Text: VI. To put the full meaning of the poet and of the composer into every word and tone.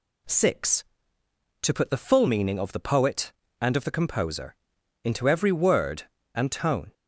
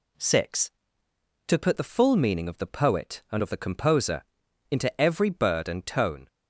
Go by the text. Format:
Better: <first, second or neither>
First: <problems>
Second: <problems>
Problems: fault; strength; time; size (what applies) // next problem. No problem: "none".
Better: first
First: pauses between "composer" and "into"; noticeable; at 4.5 s; 0.48 s long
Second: pauses between "composer" and "into"; noticeable; at 4.2 s; 0.46 s long // says "bird" for "word"; at 5.2 s